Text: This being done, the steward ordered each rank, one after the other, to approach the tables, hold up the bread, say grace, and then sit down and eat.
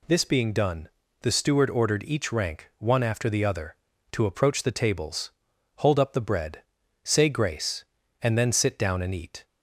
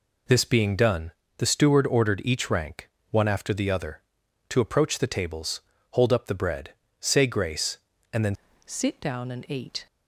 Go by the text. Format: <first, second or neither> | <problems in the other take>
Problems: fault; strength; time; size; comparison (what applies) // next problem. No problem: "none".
first | changes voice at "sit"; from 8.6 s on; 1.2 s long